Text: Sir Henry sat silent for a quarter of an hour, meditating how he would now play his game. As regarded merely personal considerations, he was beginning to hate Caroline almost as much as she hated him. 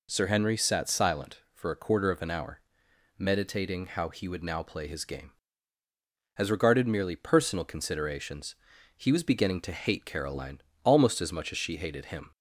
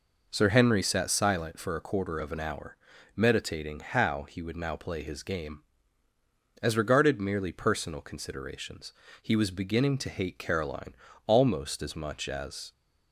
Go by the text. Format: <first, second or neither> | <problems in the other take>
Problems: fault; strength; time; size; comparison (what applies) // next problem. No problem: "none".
first | pauses between "Caroline" and "almost"; slight; at 10.9 s; 0.24 s long; slight in the first // stops before "she hated him"; at 12.7 s